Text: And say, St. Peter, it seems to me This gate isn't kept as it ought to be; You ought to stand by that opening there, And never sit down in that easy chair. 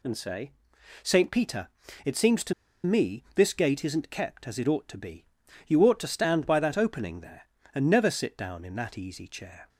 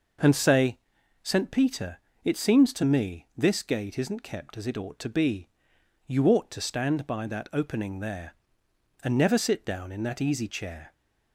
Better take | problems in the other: second | pauses between "to" and "me"; slight; at 2.5 s; 0.31 s long

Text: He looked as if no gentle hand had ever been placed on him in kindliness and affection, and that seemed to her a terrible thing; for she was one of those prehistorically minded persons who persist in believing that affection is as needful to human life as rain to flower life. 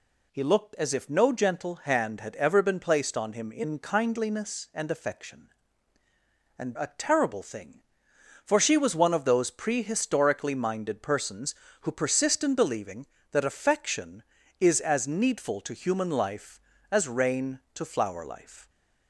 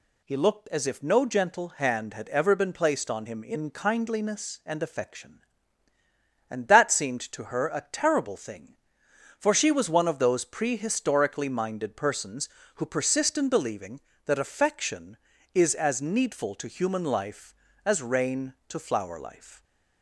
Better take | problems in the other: second | skips "that seemed to her"; at 6.7 s

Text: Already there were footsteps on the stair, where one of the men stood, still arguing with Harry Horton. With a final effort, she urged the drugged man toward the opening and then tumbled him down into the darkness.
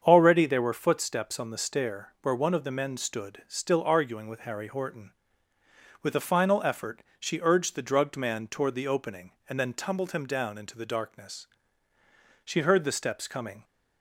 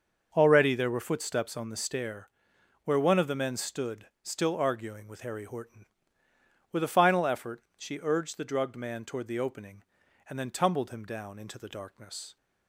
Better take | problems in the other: second | starts louder than the rest; strong; until 1.0 s; 7.5 dB; also in the second // goes on to say "She heard the steps coming"; noticeable; from 12.4 s on; 1.2 s long

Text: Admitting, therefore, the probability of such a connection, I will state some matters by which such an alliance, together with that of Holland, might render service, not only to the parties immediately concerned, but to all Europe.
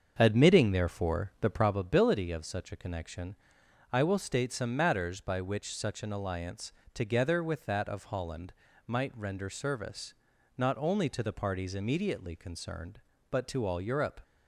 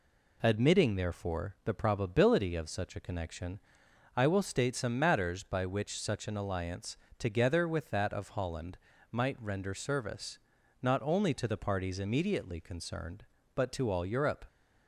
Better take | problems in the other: second | starts louder than the rest; until 1.9 s; 7 dB

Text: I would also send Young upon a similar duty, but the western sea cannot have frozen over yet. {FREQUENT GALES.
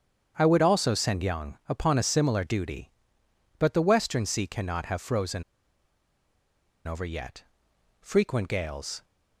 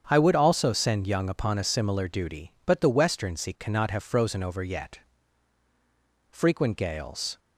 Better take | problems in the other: second | starts louder than the rest; strong; until 1.3 s; 7.5 dB; strong in the second // pauses between "frozen" and "over"; strong; at 5.4 s; 1.4 s long

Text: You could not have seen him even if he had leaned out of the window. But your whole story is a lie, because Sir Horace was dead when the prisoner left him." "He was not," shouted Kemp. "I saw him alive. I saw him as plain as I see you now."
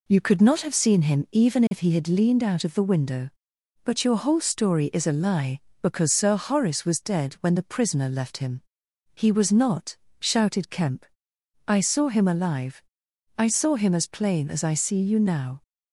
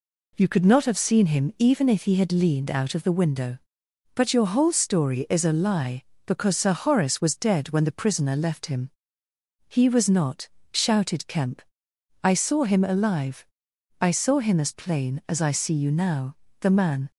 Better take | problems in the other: first | goes on to say "The man"; from 16.6 s on; 0.50 s long

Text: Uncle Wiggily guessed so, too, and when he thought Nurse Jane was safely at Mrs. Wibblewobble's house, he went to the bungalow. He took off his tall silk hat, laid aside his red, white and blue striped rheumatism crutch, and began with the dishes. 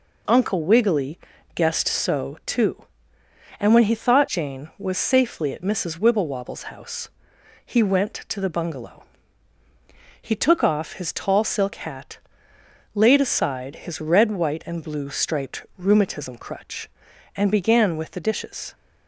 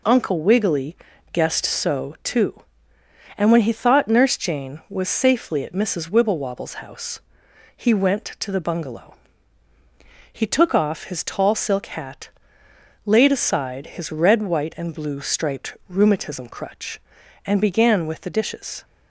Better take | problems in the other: second | pauses between "Wiggily" and "guessed"; slight; at 1.1 s; 0.34 s long; slight in the second // skips "Nurse"; at 4.2 s

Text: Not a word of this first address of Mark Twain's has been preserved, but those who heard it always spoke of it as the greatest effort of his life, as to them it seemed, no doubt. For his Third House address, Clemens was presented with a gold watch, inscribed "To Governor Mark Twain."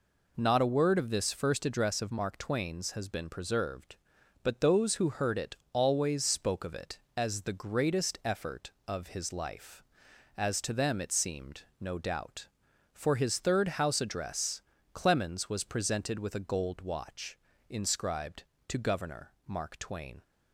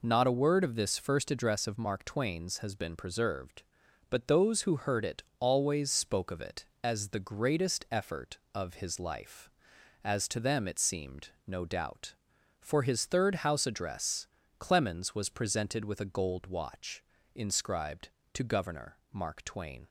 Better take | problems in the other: neither | pauses between "it" and "always"; slight; the same in both // pauses between "Governor" and "Mark"; slight; the same in both

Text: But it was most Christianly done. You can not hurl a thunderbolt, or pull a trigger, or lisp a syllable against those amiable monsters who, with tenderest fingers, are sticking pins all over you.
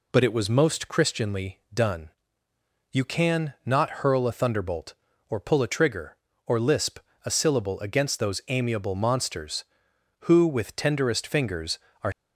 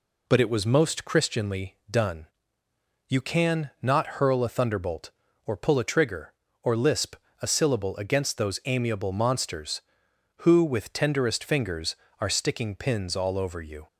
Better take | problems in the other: second | pauses between "lisp" and "a"; slight; at 6.9 s; 0.26 s long; slight in the second // stops before "sticking pins all over you"; at 12.1 s

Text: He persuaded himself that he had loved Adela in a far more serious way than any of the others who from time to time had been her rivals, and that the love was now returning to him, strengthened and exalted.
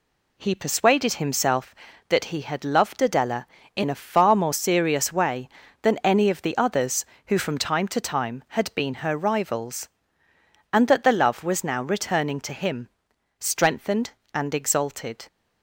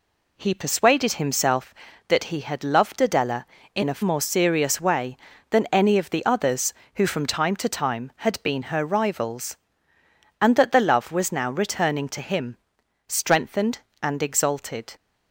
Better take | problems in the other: first | skips "far"; at 4.0 s

